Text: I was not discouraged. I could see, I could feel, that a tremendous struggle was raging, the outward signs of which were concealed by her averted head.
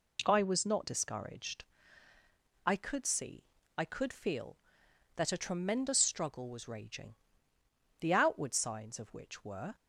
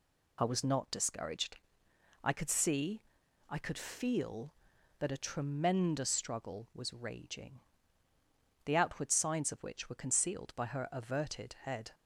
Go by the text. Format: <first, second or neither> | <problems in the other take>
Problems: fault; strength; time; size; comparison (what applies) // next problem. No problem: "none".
second | stops before "concealed by her averted head"; at 9.7 s